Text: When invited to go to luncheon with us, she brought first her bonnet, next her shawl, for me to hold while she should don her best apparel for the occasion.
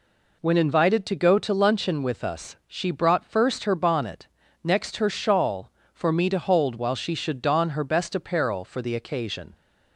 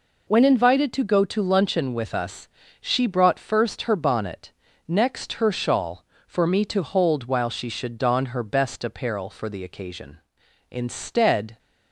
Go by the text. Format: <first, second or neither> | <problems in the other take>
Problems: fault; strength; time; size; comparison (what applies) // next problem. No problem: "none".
first | goes on to say "Instead"; noticeable; from 10.7 s on; 0.88 s long